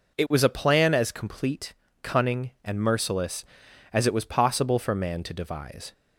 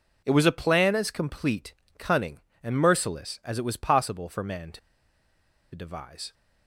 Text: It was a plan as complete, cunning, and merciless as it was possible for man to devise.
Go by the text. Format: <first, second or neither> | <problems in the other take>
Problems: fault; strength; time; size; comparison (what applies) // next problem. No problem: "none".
first | pauses between "to" and "devise"; noticeable; at 4.7 s; 0.95 s long